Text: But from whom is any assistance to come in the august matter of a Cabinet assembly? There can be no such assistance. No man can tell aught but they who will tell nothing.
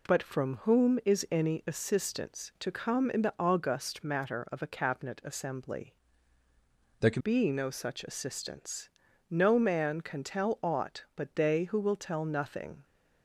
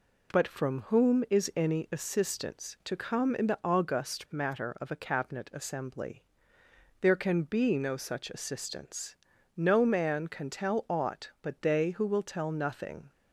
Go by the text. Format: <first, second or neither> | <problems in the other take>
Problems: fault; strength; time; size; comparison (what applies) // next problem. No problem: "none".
second | changes voice from "There" to "can"; from 6.9 to 7.2 s; 0.3 s long